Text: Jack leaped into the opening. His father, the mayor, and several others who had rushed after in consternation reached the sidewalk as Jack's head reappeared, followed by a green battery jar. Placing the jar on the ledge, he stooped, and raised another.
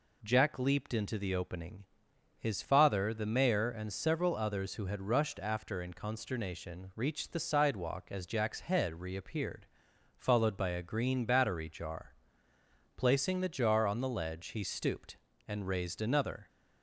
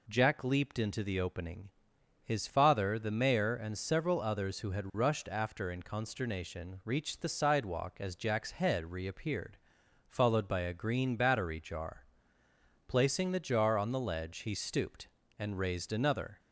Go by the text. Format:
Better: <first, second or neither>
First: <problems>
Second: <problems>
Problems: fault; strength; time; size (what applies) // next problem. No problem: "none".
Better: neither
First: none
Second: none